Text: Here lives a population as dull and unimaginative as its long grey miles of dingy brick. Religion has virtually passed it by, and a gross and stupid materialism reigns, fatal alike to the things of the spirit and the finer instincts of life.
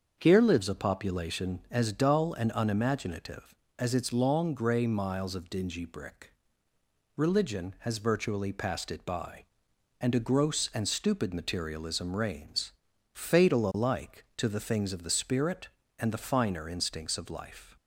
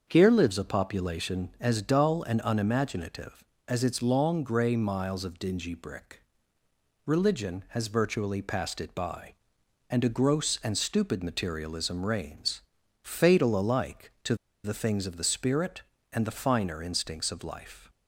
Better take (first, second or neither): first